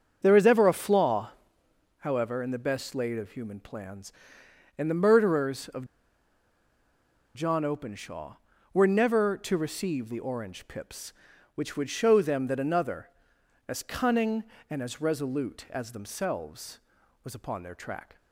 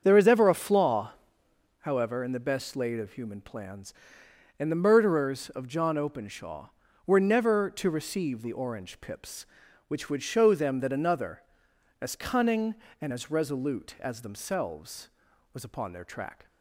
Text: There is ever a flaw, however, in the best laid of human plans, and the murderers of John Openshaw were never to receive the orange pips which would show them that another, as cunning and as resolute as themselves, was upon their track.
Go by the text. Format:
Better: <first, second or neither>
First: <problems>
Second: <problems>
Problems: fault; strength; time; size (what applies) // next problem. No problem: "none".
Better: second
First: starts louder than the rest; strong; until 1.2 s; 7 dB // pauses between "of" and "John"; strong; at 5.8 s; 1.5 s long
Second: starts louder than the rest; strong; until 1.0 s; 7 dB